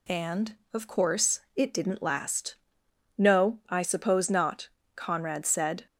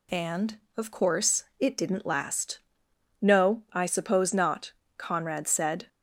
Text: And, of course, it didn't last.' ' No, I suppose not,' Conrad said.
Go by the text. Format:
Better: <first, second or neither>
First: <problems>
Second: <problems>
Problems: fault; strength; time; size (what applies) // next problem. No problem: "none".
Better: neither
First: none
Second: none